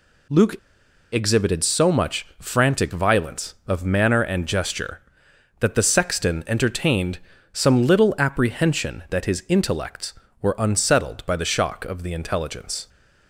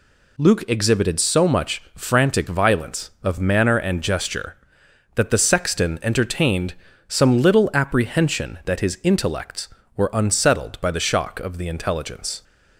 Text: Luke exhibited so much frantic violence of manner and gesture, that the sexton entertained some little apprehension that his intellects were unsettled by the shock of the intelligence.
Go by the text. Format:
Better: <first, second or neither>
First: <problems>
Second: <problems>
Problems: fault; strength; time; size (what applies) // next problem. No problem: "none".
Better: second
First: pauses between "Luke" and "exhibited"; noticeable; at 0.5 s; 0.56 s long // pauses between "entertained" and "some"; slight; at 7.1 s; 0.36 s long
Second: pauses between "entertained" and "some"; slight; at 6.7 s; 0.36 s long